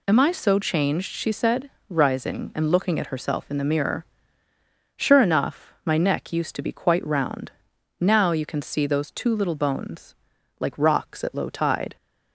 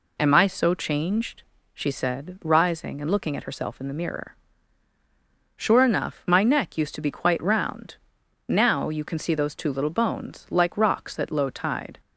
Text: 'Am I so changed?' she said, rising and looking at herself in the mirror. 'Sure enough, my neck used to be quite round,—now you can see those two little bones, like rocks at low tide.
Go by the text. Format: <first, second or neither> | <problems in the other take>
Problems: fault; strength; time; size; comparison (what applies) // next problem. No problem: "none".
neither | none